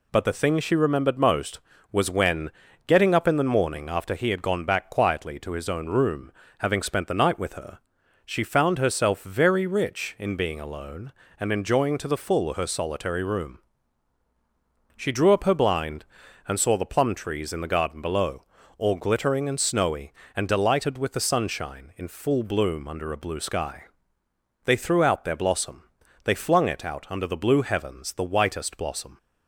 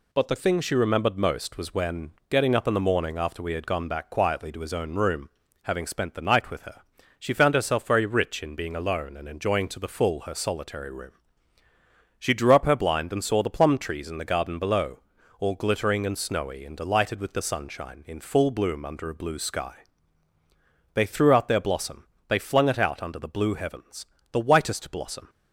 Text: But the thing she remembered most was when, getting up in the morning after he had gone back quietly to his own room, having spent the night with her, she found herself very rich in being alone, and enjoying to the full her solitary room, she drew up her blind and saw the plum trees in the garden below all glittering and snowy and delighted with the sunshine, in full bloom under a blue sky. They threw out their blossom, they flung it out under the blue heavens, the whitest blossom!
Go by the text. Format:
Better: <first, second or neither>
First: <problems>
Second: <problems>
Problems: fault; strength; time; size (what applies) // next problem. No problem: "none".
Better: first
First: pauses between "below" and "all"; slight; at 18.4 s; 0.36 s long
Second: says "we" for "he"; at 3.4 s // pauses between "below" and "all"; at 14.9 s; 0.40 s long